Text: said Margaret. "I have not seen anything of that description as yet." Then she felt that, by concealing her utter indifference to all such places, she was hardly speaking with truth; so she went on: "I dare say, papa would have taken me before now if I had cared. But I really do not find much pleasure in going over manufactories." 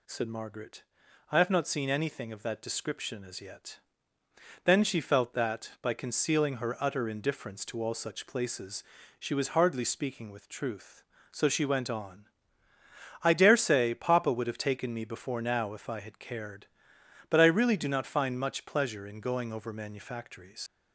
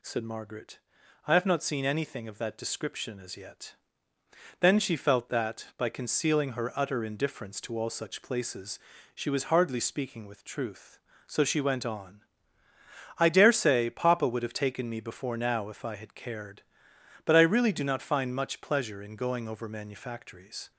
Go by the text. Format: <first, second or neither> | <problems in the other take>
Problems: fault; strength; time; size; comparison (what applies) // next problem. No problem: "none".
second | leaves "manufactories" unfinished; at 20.6 s; 90 ms